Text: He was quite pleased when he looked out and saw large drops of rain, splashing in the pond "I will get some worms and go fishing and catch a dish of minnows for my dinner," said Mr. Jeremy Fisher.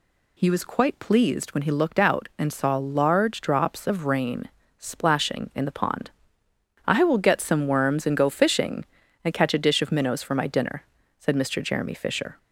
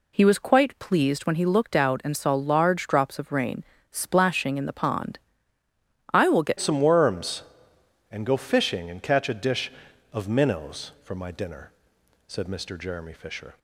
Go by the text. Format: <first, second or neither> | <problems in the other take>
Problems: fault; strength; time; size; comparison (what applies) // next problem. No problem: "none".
first | pauses between "pond" and "I"; noticeable; at 5.1 s; 0.94 s long; noticeable in the first // changes voice at "some"; from 6.5 s on; 7.0 s long